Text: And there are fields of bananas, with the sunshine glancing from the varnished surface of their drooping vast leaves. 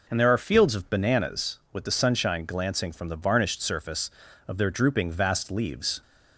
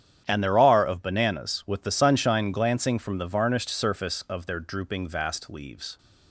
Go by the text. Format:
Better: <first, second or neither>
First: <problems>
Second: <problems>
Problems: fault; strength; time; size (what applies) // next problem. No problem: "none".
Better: first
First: none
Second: starts louder than the rest; strong; until 1.2 s; 9.5 dB // skips "fields"; at 0.8 s